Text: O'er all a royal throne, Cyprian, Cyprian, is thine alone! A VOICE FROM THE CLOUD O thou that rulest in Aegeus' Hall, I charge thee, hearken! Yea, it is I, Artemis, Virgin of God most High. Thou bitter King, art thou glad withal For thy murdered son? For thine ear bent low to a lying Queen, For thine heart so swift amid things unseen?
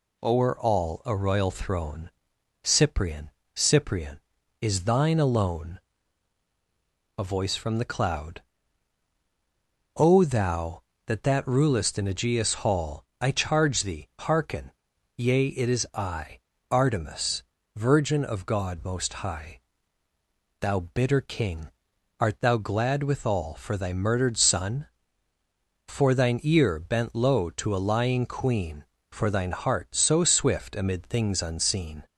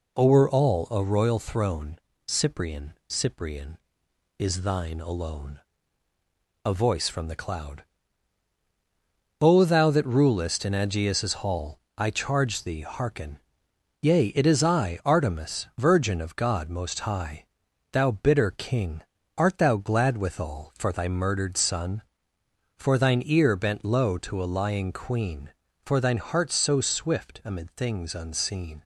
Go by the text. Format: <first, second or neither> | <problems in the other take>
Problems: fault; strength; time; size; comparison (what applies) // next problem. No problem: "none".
second | pauses between "CLOUD" and "O"; strong; at 8.4 s; 1.5 s long; strong in the second // says "that" twice; at 11.2 s